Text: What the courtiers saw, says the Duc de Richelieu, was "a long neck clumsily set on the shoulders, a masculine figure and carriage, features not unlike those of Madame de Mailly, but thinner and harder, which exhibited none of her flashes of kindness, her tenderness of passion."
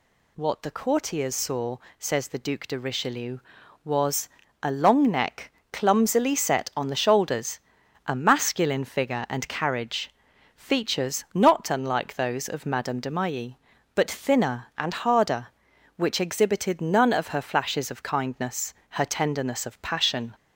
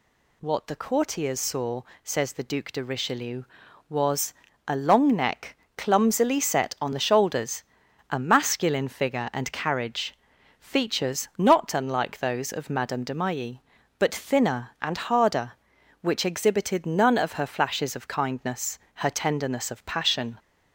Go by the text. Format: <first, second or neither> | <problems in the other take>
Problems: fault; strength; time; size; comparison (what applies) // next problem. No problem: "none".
neither | pauses between "was" and "a"; slight; the same in both // pauses between "neck" and "clumsily"; slight; the same in both